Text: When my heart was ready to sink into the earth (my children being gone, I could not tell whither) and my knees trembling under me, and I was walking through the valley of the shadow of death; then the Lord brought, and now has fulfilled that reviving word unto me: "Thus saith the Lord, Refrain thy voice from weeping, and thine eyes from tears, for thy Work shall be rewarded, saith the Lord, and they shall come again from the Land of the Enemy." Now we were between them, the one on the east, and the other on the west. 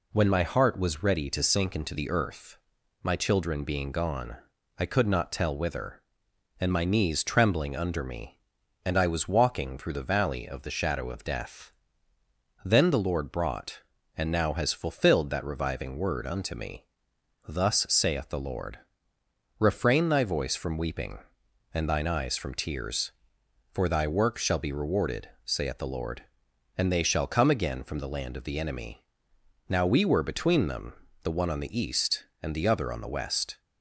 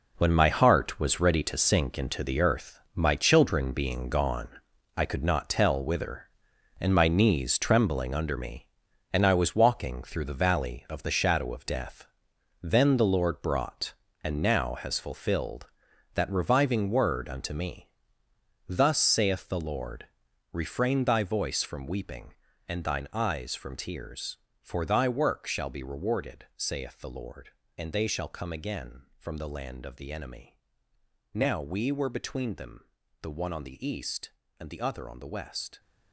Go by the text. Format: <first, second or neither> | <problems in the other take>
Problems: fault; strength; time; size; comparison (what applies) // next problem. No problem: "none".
first | gets quieter; strong; throughout; 11 dB